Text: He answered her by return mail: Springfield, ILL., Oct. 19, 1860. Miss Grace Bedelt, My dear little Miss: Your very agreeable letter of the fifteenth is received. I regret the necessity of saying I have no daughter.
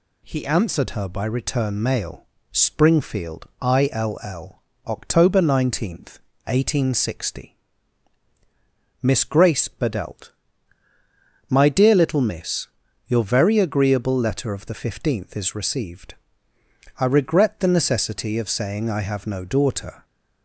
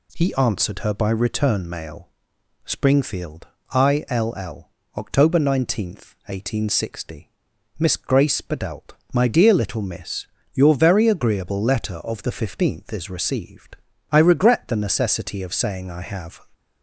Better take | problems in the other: first | stops before "no daughter"; at 16.5 s

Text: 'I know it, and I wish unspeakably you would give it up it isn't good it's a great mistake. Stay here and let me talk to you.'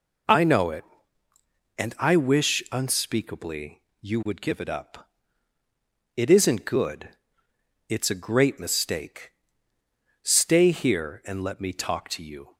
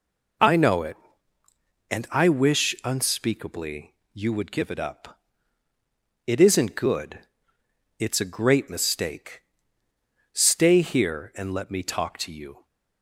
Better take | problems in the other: neither | pauses between "unspeakably" and "you"; slight; the same in both // pauses between "up" and "it"; the same in both // pauses between "good" and "it's"; noticeable; the same in both

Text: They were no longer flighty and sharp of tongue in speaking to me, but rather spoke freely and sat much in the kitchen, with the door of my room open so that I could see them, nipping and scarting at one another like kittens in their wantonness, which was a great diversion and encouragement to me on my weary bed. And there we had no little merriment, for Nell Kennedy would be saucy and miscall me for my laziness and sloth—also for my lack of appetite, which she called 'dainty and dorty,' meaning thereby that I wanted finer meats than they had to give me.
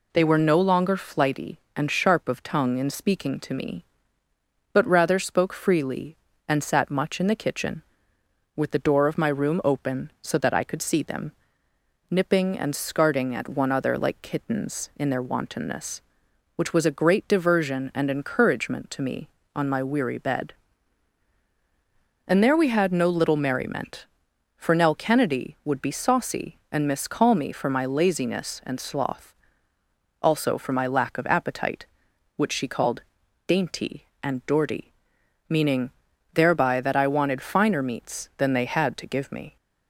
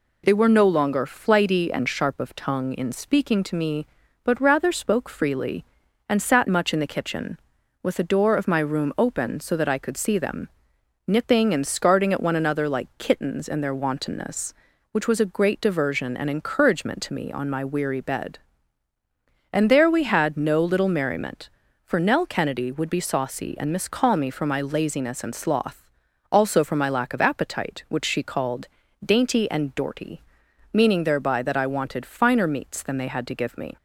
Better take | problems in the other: second | says "other" for "another"; at 13.7 s // pauses between "called" and "dainty"; at 33.0 s; 0.44 s long; also in the second // pauses between "meaning" and "thereby"; at 35.9 s; 0.44 s long

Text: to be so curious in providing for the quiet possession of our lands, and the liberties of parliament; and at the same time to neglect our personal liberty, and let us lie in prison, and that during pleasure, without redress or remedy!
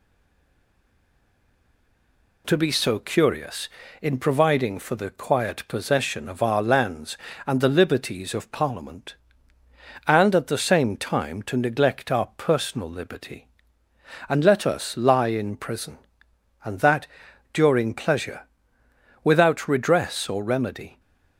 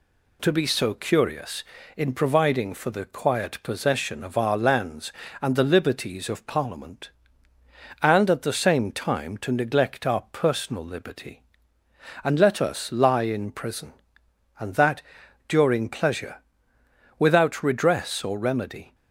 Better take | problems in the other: second | stays silent before the first word; until 2.4 s; 2.4 s long // pauses between "that" and "during"; at 17.0 s; 0.44 s long; also in the second

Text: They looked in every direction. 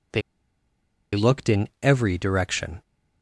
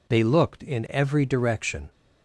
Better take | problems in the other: second | pauses between "They" and "looked"; noticeable; at 0.2 s; 0.94 s long

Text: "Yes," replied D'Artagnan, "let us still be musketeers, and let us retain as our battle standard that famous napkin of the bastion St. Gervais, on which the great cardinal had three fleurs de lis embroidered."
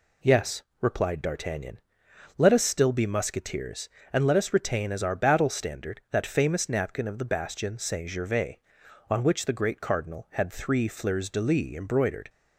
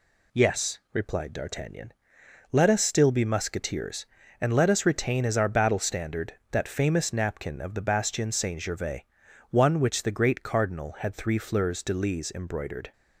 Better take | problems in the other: first | says "one" for "on"; at 9.4 s

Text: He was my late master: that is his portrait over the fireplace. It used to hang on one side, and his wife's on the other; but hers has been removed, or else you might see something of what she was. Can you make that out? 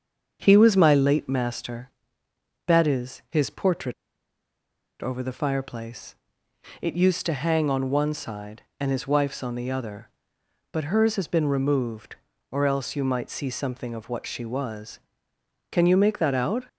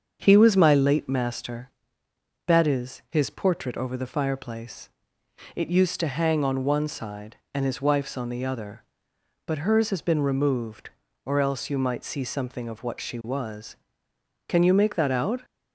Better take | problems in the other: second | starts louder than the rest; until 1.4 s; 7 dB; also in the second // pauses between "portrait" and "over"; at 3.9 s; 1.0 s long

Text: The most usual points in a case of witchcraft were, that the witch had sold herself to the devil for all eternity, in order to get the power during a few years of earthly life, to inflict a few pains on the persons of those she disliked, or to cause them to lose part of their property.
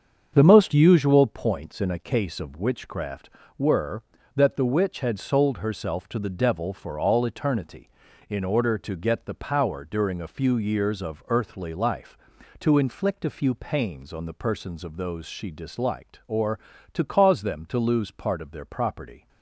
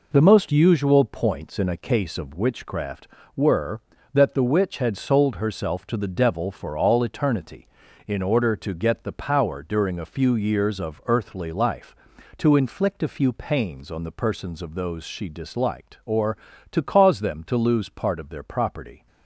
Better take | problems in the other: second | starts louder than the rest; strong; until 1.3 s; 7 dB

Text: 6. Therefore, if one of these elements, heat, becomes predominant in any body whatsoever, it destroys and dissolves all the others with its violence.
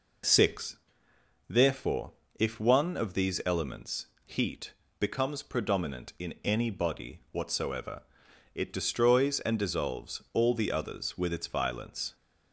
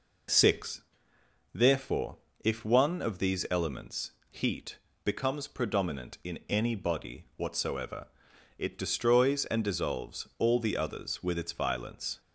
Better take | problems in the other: neither | none

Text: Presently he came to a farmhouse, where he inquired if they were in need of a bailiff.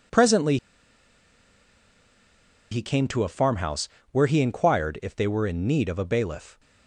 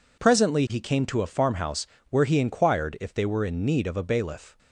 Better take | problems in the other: second | pauses between "Presently" and "he"; strong; at 0.5 s; 2.1 s long

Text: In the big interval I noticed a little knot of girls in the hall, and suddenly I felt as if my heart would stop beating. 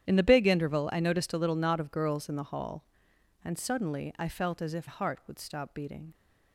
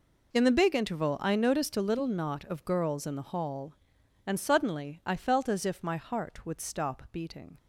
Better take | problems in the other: second | starts louder than the rest; strong; until 1.1 s; 10 dB // skips "my"; at 4.8 s

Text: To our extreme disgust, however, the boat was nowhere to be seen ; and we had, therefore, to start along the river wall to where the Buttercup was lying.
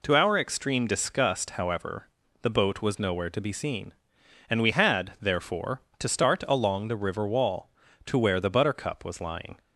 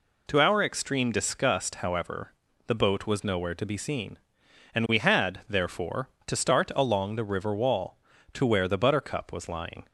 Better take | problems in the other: neither | none

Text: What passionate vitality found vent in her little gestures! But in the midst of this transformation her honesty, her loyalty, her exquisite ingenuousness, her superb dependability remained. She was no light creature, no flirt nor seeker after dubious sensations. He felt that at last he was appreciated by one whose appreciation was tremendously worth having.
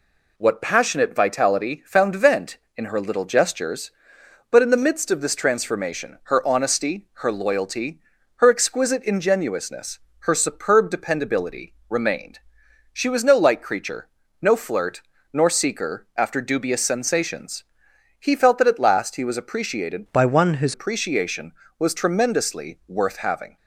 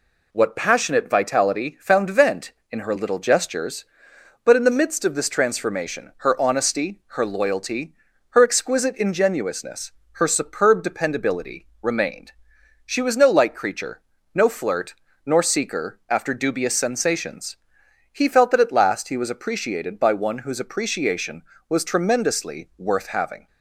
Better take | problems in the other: second | pauses between "flirt" and "nor"; slight; at 15.0 s; 0.30 s long; slight in the second // changes voice from "by" to "whose"; from 20.1 to 20.7 s; 0.6 s long

